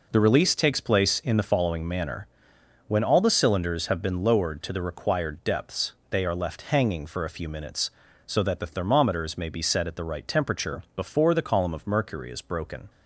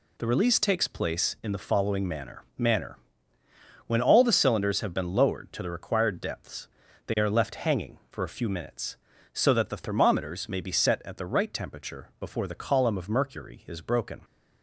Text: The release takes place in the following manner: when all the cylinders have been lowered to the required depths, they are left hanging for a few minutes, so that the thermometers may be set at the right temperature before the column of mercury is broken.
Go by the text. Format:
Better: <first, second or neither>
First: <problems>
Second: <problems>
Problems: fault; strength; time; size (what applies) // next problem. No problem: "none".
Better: first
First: none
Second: says "manner" twice; at 2.5 s